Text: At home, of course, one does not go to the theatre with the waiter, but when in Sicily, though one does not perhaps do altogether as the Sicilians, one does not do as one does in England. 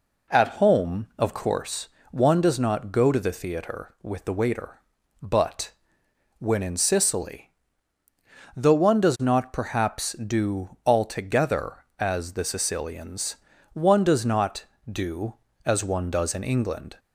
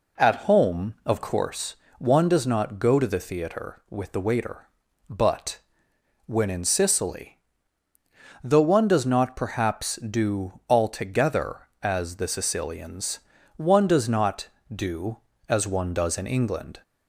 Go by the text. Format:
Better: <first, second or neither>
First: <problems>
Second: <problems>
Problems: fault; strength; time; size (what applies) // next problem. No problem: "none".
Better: neither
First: pauses between "but" and "when"; noticeable; at 5.7 s; 0.66 s long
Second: pauses between "but" and "when"; noticeable; at 5.5 s; 0.66 s long